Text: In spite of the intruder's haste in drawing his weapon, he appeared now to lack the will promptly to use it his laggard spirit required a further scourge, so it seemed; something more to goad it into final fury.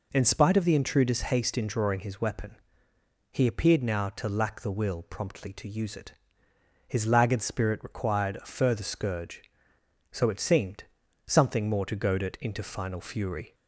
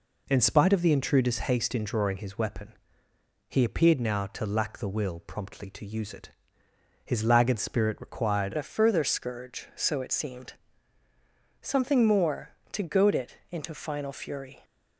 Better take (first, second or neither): first